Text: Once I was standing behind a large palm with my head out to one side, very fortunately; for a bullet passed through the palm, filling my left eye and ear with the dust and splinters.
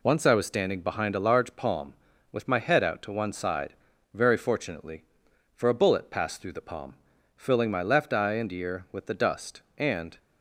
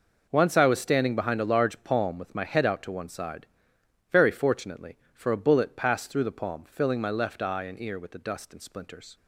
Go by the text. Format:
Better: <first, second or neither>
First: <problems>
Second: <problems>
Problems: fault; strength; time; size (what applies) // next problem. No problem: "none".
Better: second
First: stops before "splinters"; at 10.1 s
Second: none